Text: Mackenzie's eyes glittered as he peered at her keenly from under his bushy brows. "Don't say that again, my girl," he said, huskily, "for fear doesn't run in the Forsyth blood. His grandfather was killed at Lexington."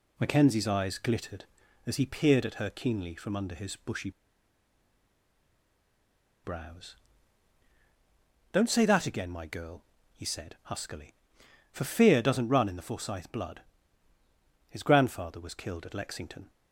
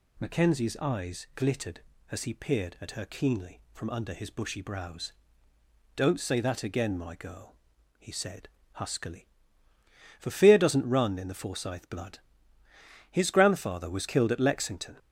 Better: second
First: pauses between "bushy" and "brows"; strong; at 4.1 s; 2.3 s long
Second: none

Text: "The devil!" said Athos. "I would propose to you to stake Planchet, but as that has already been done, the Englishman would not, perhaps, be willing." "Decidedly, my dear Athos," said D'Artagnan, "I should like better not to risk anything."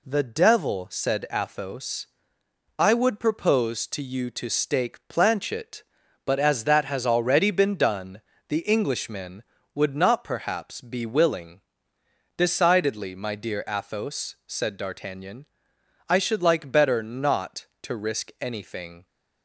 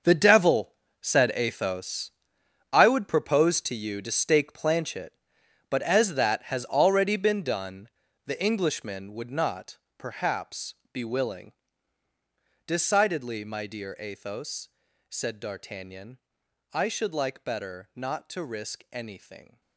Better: first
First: none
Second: gets quieter; strong; throughout; 13 dB

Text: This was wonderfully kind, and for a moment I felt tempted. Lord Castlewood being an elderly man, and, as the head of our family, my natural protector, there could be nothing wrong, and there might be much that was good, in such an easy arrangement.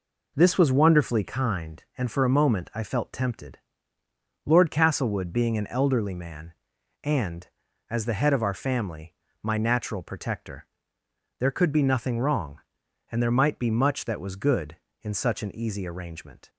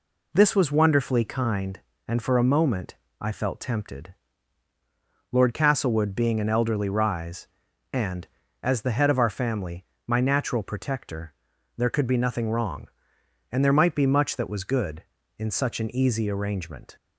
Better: first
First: none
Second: pauses between "moment" and "I"; slight; at 2.9 s; 0.24 s long // says "rise" for "man"; at 6.8 s

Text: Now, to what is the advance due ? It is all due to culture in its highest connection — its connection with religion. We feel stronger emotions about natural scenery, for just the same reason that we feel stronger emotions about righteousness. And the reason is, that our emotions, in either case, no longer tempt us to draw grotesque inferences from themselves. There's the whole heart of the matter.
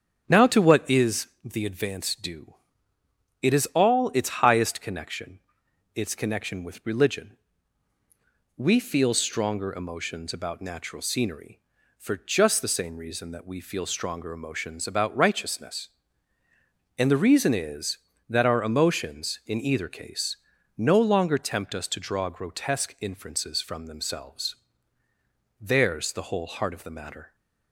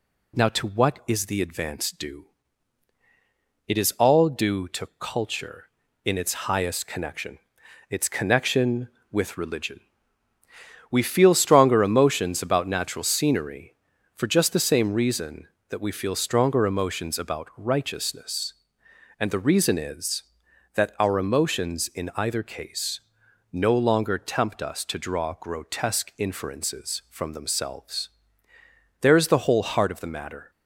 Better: second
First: starts louder than the rest; strong; until 1.2 s; 7 dB // pauses between "is" and "the"; slight; at 1.2 s; 0.16 s long // skips "due to culture in"; at 4.1 s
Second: none

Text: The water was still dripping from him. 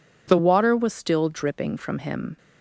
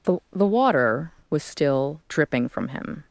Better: first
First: none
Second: says "The" twice; at 0.3 s

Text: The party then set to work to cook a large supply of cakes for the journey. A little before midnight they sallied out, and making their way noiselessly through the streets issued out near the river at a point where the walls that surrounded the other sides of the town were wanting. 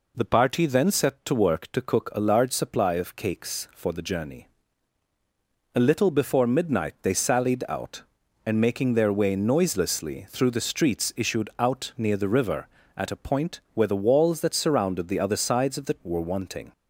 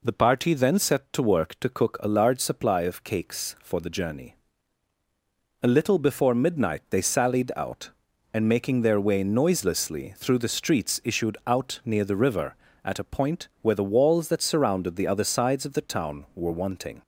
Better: second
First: skips "town"; at 16.0 s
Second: none

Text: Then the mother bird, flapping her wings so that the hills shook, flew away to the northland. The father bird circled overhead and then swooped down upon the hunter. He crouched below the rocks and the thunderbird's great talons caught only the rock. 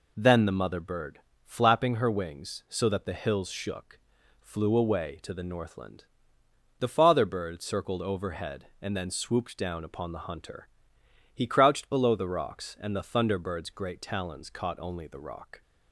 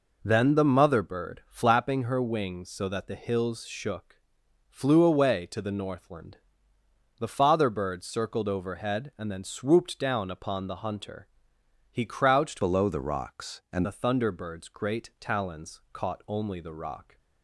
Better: first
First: none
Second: changes voice from "below" to "and"; from 12.6 to 13.8 s; 1.2 s long

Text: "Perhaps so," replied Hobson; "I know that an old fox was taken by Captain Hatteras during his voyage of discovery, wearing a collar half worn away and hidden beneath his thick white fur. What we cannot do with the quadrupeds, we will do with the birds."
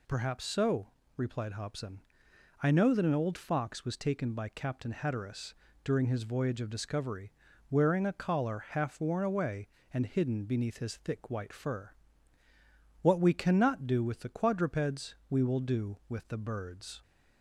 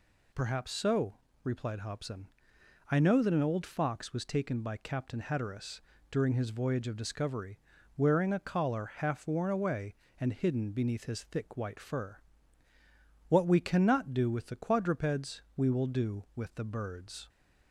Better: neither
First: pauses between "Hatteras" and "during"; slight; at 5.5 s; 0.28 s long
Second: pauses between "Hatteras" and "during"; slight; at 5.8 s; 0.28 s long

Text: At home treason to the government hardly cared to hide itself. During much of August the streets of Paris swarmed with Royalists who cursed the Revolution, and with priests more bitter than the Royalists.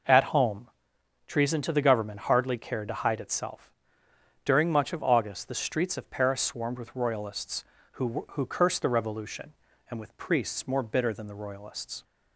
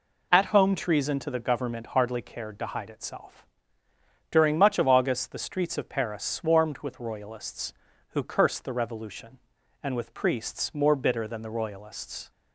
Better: second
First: pauses between "home" and "treason"; noticeable; at 0.6 s; 0.58 s long // says "who" twice; at 8.3 s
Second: none

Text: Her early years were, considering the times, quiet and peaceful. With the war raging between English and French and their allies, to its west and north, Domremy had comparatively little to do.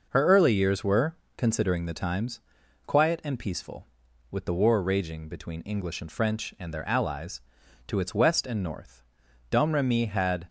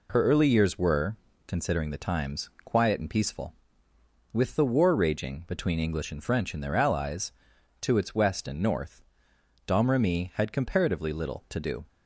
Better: second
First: stops before "comparatively little to do"; at 10.4 s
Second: none

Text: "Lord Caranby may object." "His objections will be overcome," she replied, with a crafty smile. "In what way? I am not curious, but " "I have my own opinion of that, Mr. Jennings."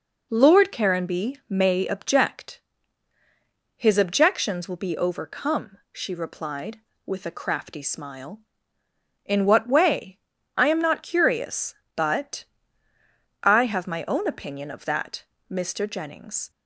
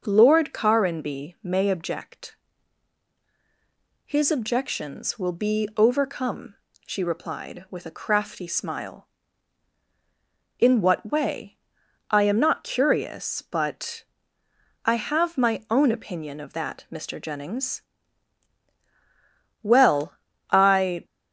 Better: first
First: none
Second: goes on to say "Well I"; from 19.6 s on; 1.4 s long

